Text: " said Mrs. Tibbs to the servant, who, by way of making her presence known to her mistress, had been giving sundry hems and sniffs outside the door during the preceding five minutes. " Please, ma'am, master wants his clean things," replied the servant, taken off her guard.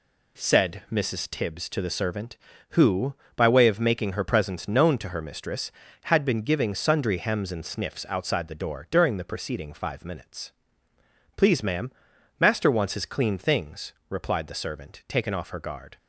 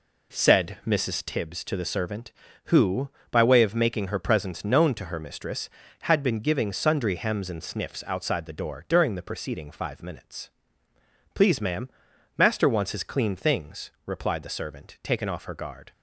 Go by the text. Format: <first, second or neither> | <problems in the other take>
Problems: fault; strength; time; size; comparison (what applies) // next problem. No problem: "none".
first | starts louder than the rest; slight; until 1.4 s; 3.5 dB